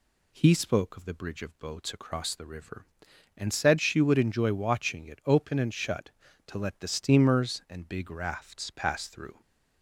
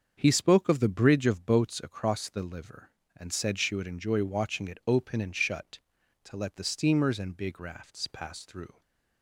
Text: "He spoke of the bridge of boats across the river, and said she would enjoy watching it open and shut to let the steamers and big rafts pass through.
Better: first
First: none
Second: starts louder than the rest; until 1.1 s; 7 dB // says "liver" for "river"; at 2.4 s // stays silent after the last word; slight; from 8.7 s on; 0.5 s long

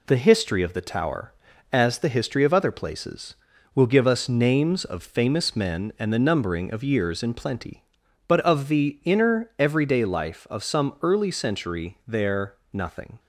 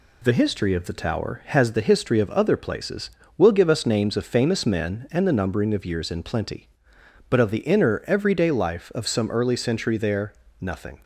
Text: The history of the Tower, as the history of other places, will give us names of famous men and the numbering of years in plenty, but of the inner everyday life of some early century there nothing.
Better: first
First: pauses between "there" and "nothing"; slight; at 12.5 s; 0.18 s long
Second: says "has" for "as"; at 1.4 s // pauses between "there" and "nothing"; slight; at 10.3 s; 0.28 s long

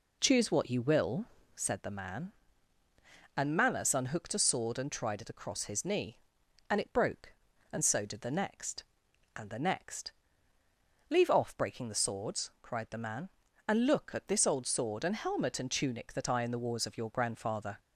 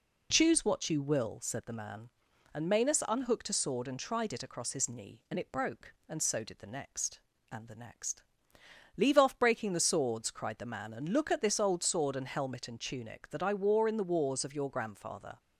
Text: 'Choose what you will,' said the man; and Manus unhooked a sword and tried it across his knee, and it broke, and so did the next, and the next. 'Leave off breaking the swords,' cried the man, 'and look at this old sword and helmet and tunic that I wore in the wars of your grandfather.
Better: second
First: skips "wore"; at 16.4 s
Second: none

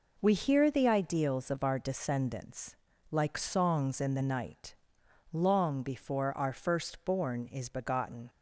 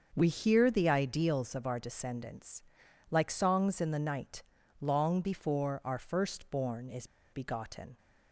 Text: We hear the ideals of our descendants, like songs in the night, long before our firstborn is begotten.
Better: first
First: none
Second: starts louder than the rest; until 1.1 s; 6.5 dB // pauses between "is" and "begotten"; slight; at 7.0 s; 0.25 s long

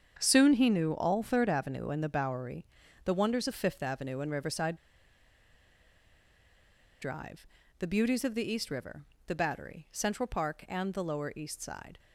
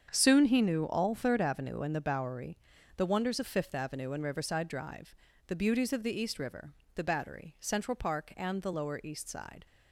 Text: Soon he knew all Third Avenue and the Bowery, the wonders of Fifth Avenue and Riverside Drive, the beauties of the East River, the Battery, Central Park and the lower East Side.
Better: second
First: starts louder than the rest; strong; until 1.2 s; 7.5 dB // pauses between "Riverside" and "Drive"; strong; at 4.7 s; 2.2 s long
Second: starts louder than the rest; strong; until 1.1 s; 7.5 dB

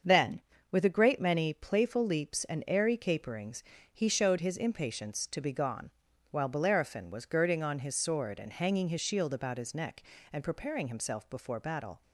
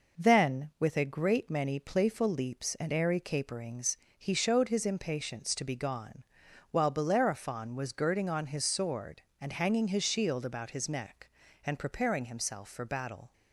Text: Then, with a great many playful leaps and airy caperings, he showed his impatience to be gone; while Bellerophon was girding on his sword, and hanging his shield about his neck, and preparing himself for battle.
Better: second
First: starts louder than the rest; until 1.3 s; 7 dB // says "before" for "for"; at 11.2 s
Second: none

